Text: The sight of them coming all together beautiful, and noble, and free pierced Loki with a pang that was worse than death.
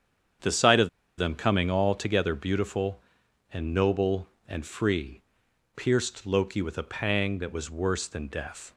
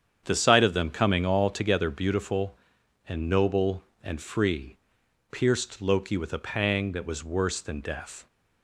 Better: second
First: starts louder than the rest; strong; until 1.7 s; 8 dB // pauses between "of" and "them"; slight; at 0.8 s; 0.30 s long // pauses between "free" and "pierced"; noticeable; at 5.2 s; 0.54 s long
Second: starts louder than the rest; strong; until 1.2 s; 8 dB // pauses between "free" and "pierced"; noticeable; at 4.7 s; 0.54 s long

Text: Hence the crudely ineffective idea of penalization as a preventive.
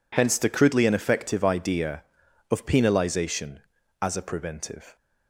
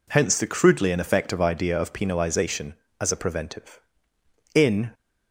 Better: first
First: none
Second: goes on to say "In"; slight; from 4.5 s on; 0.36 s long

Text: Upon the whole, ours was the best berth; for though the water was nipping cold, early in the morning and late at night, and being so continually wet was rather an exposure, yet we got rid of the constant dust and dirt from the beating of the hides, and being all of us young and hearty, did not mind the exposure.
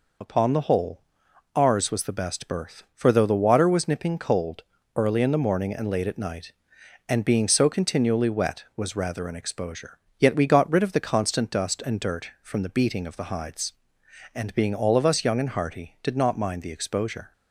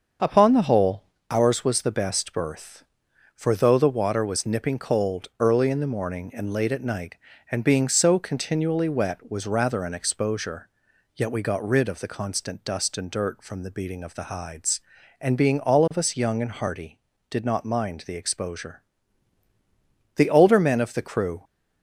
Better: first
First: none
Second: starts louder than the rest; until 1.4 s; 6.5 dB // goes on to say "The older men of the crew"; noticeable; from 20.1 s on; 1.2 s long

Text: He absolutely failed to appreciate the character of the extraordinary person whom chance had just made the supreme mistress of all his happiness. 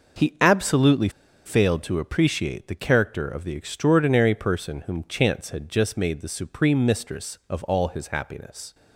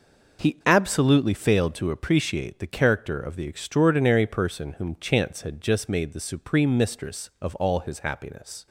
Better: second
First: pauses between "absolutely" and "failed"; at 1.0 s; 0.36 s long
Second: none

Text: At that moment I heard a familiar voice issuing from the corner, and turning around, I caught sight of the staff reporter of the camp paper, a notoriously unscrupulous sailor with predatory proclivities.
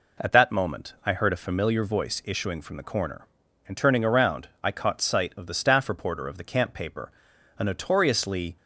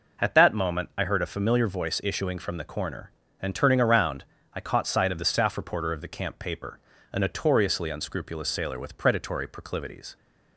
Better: second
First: stops before "unscrupulous sailor with predatory proclivities"; at 8.5 s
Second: none

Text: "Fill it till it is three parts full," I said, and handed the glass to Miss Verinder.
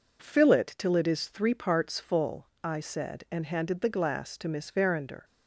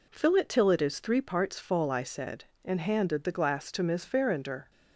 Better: neither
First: none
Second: none

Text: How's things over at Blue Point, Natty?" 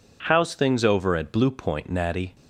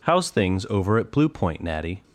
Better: neither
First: none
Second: none

